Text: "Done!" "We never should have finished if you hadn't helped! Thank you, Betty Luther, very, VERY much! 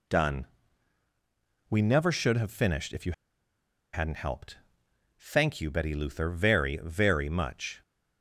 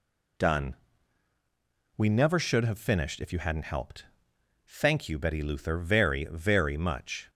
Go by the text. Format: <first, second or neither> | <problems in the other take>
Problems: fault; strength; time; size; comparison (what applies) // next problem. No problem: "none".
second | pauses between "you" and "hadn't"; noticeable; at 3.1 s; 0.80 s long